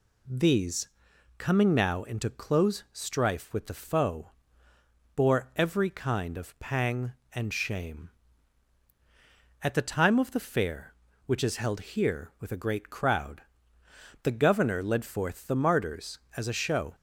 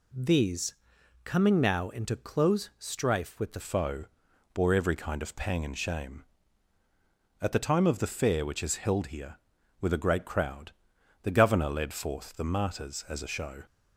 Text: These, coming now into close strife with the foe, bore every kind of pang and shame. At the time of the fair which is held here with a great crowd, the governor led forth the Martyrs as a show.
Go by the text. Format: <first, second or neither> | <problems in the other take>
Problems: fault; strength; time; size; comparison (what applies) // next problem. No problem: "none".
first | changes voice at "foe"; from 3.6 s on; 10.0 s long